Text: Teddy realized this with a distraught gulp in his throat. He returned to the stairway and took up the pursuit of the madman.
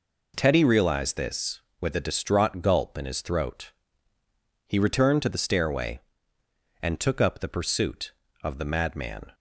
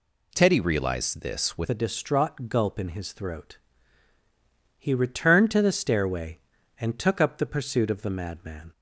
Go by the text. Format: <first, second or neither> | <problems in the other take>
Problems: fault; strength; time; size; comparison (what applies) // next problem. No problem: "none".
first | changes voice at "a"; from 1.6 s on; 7.1 s long